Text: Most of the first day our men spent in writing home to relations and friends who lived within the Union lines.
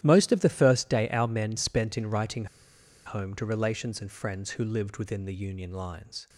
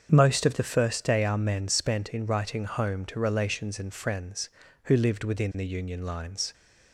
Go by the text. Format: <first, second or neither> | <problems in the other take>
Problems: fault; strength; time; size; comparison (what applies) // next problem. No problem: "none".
second | starts louder than the rest; strong; until 1.0 s; 12.5 dB; strong in the second // pauses between "writing" and "home"; noticeable; at 2.4 s; 0.60 s long